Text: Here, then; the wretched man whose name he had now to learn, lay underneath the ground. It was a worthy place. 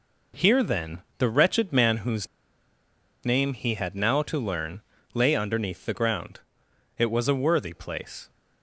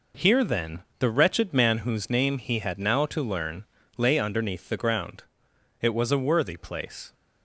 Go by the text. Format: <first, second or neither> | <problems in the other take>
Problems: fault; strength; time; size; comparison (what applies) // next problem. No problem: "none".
second | pauses between "whose" and "name"; noticeable; at 2.2 s; 0.96 s long